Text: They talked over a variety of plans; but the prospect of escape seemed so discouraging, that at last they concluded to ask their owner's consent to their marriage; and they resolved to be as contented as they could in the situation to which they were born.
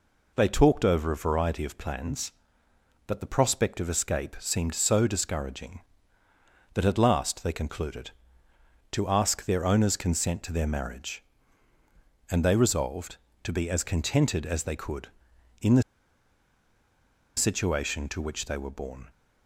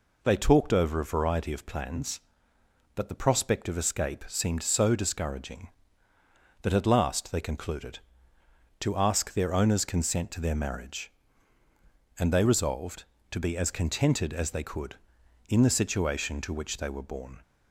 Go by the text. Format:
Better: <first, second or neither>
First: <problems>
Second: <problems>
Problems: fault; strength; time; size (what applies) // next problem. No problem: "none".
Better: second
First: pauses between "the" and "situation"; strong; at 15.8 s; 1.5 s long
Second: none